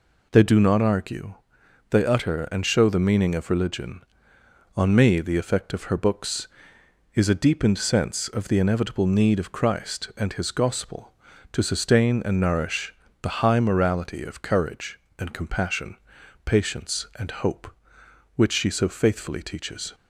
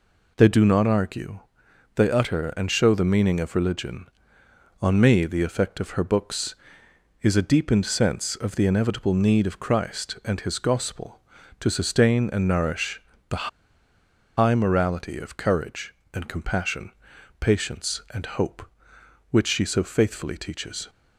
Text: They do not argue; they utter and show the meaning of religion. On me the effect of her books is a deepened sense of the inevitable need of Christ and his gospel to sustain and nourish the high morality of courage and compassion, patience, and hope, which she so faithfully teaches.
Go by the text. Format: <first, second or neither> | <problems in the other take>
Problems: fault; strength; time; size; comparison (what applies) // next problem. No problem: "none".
first | pauses between "nourish" and "the"; slight; at 12.9 s; 0.30 s long; slight in the first // pauses between "the" and "high"; noticeable; at 13.4 s; 0.89 s long